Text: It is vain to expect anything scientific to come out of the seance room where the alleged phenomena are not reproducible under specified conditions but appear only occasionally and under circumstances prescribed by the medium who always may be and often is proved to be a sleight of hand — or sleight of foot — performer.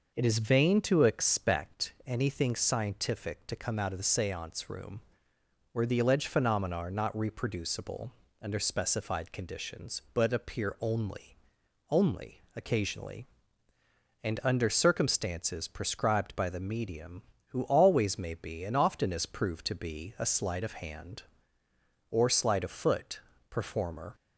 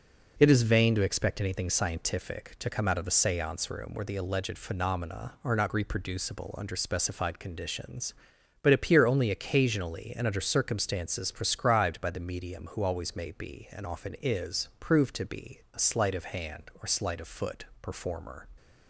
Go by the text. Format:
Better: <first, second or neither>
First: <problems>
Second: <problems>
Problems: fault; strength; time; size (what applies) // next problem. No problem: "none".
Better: second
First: pauses between "room" and "where"; noticeable; at 5.0 s; 0.70 s long // pauses between "reproducible" and "under"; slight; at 8.1 s; 0.28 s long // says "only" twice; at 11.8 s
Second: none